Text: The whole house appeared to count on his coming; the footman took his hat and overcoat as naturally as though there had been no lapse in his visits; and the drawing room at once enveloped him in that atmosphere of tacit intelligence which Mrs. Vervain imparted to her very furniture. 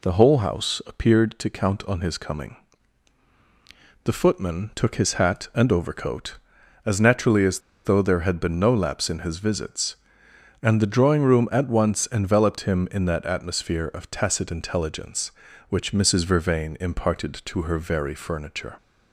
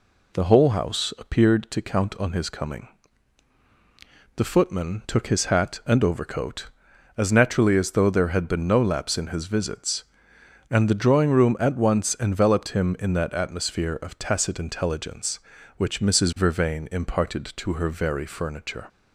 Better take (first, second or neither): second